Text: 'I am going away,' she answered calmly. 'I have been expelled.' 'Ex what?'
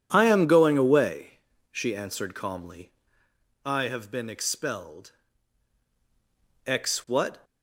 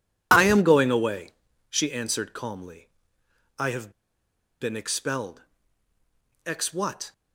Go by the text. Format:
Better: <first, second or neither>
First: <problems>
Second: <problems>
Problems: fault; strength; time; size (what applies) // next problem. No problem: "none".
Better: first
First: none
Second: pauses between "have" and "been"; noticeable; at 3.9 s; 0.68 s long